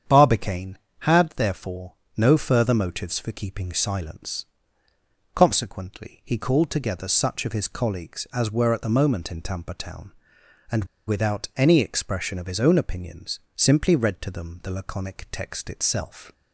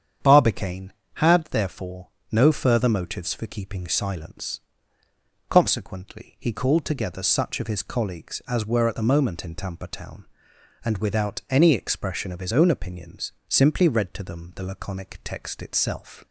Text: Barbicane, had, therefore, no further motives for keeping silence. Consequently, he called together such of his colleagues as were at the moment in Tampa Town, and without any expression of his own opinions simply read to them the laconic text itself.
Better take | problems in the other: second | starts louder than the rest; strong; until 1.3 s; 8 dB; strong in the second // pauses between "and" and "without"; slight; at 10.8 s; 0.22 s long // pauses between "opinions" and "simply"; slight; at 13.3 s; 0.16 s long; slight in the second

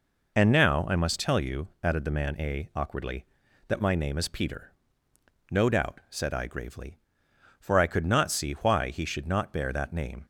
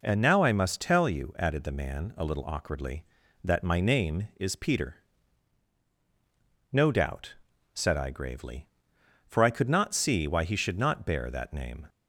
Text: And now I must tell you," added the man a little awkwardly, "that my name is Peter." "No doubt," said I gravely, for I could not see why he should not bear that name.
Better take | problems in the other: second | skips "little"; at 2.7 s

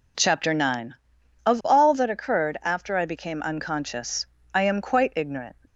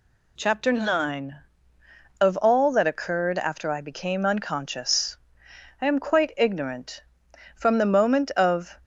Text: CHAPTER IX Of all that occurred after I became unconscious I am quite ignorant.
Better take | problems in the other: first | pauses between "unconscious" and "I"; noticeable; at 5.1 s; 0.64 s long; slight in the first // goes on to say "From the moment of"; noticeable; from 7.5 s on; 1.2 s long

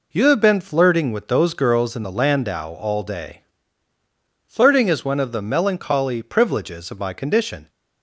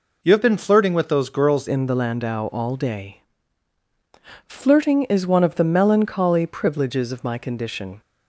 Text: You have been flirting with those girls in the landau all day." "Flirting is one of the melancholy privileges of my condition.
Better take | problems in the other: first | changes voice at "in"; from 1.6 s on; 6.4 s long

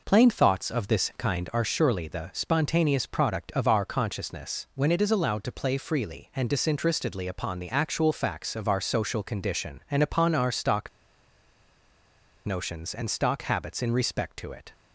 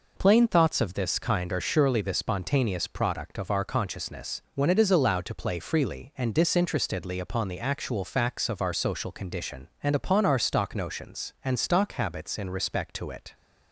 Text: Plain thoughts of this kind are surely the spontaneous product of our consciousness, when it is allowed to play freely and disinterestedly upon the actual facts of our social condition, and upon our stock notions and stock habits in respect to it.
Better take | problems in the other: second | pauses between "stock" and "notions"; strong; at 10.8 s; 1.5 s long

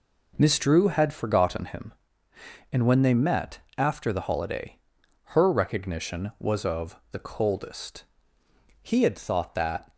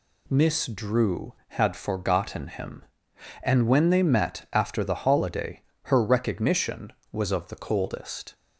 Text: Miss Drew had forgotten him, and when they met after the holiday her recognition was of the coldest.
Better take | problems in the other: second | pauses between "met" and "after"; slight; at 3.6 s; 0.18 s long // pauses between "holiday" and "her"; noticeable; at 4.7 s; 0.50 s long; slight in the second // goes on to say "He had thought that"; noticeable; from 8.8 s on; 1.1 s long

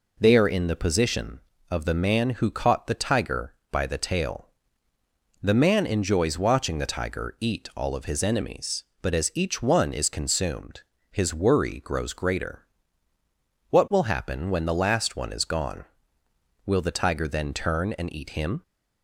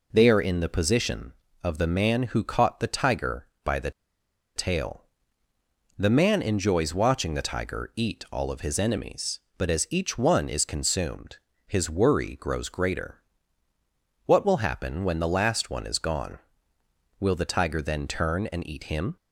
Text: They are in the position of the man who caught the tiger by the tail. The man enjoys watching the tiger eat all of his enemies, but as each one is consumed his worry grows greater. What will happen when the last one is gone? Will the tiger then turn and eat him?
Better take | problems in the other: first | pauses between "the" and "tail"; noticeable; at 3.9 s; 0.64 s long // pauses between "consumed" and "his"; slight; at 11.3 s; 0.30 s long; slight in the first

